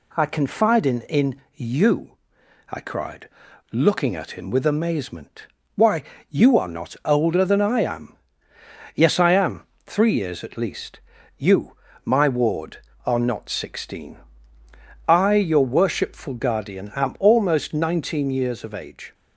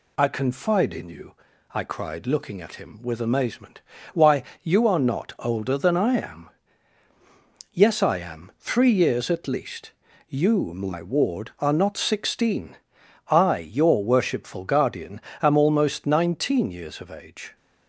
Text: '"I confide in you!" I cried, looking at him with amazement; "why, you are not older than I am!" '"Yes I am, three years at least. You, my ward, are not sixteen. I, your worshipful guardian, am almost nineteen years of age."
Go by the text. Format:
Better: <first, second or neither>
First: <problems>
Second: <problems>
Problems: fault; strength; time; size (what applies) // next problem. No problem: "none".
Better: second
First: says "in" twice; at 1.0 s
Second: none